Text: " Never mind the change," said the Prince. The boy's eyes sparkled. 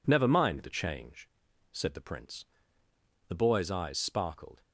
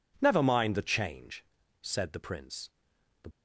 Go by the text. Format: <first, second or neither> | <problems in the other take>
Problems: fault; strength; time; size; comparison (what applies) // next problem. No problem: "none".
first | stops before "boy's eyes sparkled"; at 3.3 s